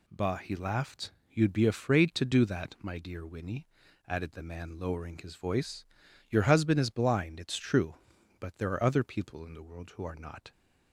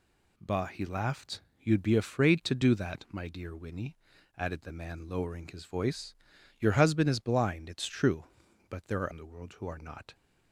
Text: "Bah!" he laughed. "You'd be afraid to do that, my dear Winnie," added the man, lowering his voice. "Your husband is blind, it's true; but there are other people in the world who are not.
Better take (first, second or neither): first